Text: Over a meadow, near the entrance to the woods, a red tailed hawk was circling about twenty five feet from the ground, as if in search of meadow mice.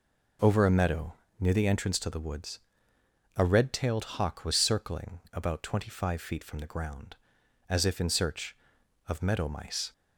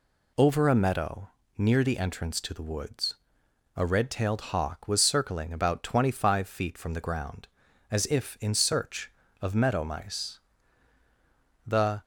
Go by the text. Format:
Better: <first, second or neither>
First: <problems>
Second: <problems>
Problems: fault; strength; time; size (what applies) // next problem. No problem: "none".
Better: first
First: none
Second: goes on to say "The"; slight; from 11.6 s on; 0.36 s long